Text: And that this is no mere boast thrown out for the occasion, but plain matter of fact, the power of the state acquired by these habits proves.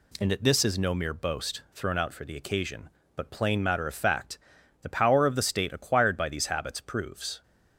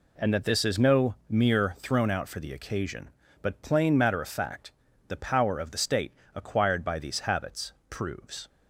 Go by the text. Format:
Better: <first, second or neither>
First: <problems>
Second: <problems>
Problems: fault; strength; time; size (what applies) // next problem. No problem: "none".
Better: first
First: none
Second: skips "boast"; at 1.7 s // pauses between "state" and "acquired"; slight; at 6.1 s; 0.24 s long // pauses between "habits" and "proves"; slight; at 7.7 s; 0.18 s long